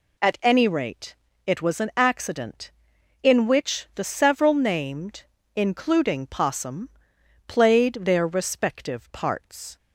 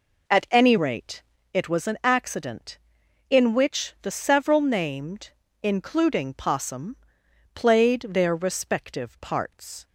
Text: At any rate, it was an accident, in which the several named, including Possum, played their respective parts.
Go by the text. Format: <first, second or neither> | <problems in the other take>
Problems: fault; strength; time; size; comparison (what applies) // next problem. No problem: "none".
first | starts louder than the rest; noticeable; until 1.5 s; 4 dB